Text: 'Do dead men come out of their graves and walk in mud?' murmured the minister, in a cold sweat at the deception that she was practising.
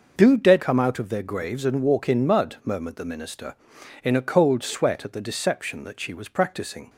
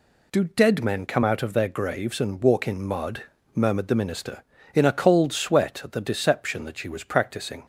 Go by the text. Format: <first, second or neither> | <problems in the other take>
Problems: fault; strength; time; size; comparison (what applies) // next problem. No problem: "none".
second | skips "men"; at 0.6 s